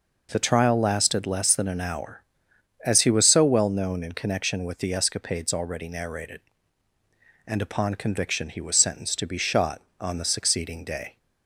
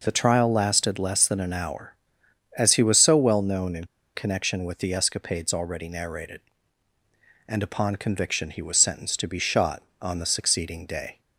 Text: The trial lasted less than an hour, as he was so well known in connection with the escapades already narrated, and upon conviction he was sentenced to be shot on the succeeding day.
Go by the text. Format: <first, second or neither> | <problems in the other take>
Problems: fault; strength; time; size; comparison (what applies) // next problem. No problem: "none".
first | pauses between "in" and "connection"; slight; at 3.8 s; 0.30 s long